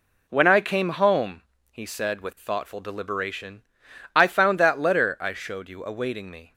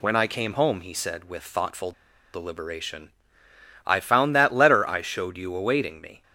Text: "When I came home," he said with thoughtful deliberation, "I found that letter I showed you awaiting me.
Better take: first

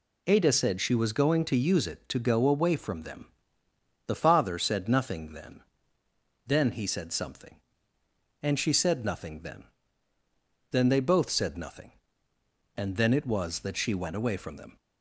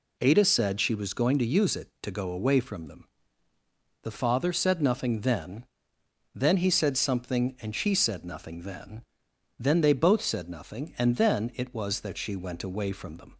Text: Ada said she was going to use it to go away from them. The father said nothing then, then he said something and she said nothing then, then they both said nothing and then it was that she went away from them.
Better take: neither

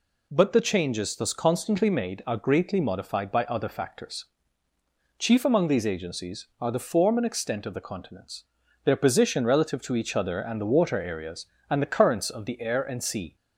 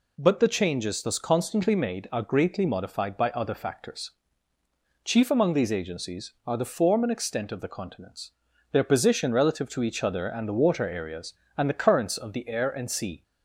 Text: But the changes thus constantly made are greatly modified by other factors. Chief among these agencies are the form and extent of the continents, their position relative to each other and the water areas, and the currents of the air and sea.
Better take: neither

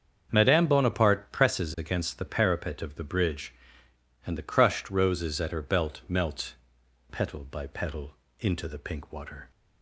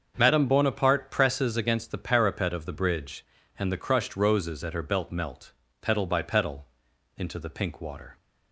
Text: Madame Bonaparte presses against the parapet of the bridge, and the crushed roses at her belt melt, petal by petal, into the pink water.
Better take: neither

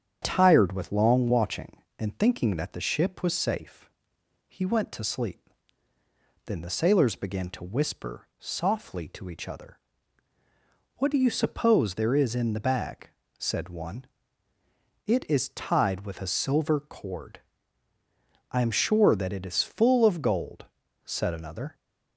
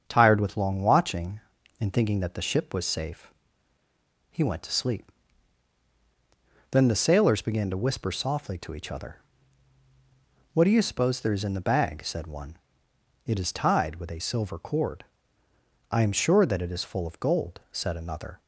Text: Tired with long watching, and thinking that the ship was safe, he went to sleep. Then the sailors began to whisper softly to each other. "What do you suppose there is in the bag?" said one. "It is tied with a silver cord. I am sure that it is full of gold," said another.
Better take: neither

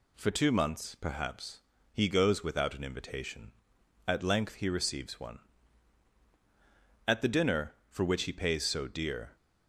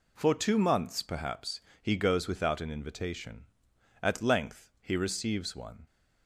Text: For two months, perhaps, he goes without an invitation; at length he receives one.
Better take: second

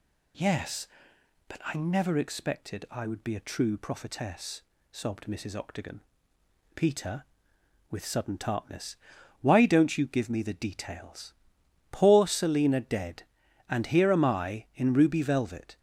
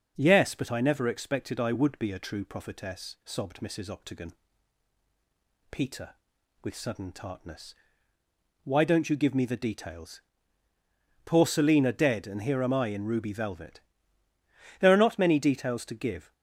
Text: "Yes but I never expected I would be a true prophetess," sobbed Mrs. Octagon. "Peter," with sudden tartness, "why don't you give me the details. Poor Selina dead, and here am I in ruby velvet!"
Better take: first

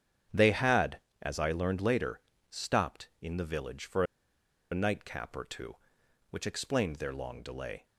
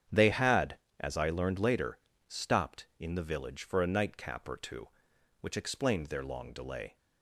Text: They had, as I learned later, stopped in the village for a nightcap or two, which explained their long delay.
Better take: second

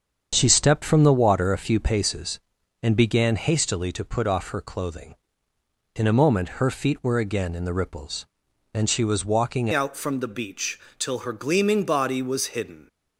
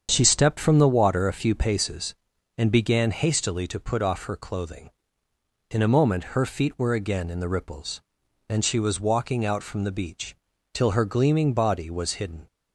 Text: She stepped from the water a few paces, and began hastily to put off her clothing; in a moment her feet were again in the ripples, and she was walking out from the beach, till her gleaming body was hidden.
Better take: second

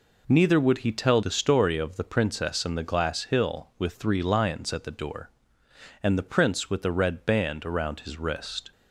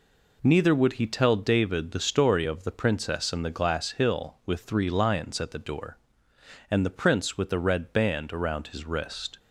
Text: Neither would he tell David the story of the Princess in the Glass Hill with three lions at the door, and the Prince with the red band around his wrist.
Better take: second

